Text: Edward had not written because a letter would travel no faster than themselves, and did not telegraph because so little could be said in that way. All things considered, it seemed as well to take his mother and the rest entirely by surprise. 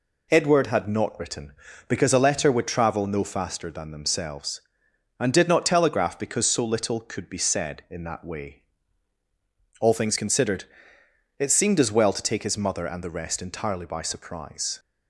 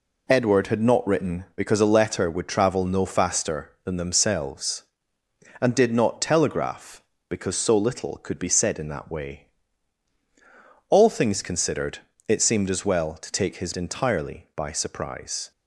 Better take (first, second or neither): first